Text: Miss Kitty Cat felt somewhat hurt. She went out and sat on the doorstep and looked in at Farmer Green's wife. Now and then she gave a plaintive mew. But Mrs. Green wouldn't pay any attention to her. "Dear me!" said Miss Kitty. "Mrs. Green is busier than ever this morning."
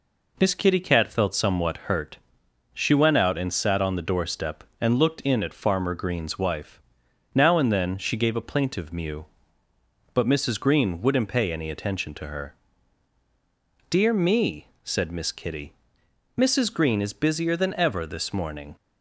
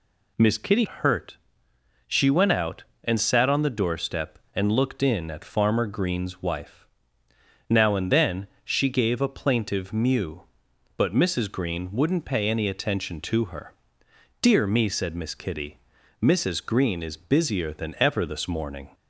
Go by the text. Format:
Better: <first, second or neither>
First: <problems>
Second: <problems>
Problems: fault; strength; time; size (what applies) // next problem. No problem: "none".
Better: first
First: none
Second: skips "Cat felt somewhat"; at 0.8 s // pauses between "then" and "she"; slight; at 8.4 s; 0.16 s long